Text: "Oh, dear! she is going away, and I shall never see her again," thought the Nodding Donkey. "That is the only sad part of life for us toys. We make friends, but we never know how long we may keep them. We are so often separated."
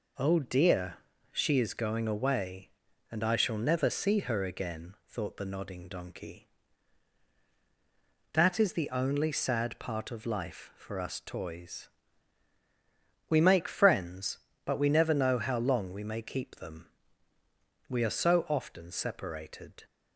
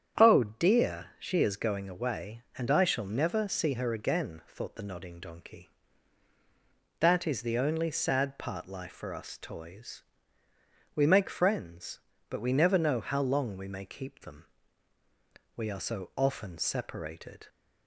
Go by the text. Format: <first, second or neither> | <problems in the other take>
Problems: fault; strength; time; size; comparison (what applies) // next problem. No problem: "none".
first | starts louder than the rest; strong; until 1.4 s; 8.5 dB // skips "of"; at 8.6 s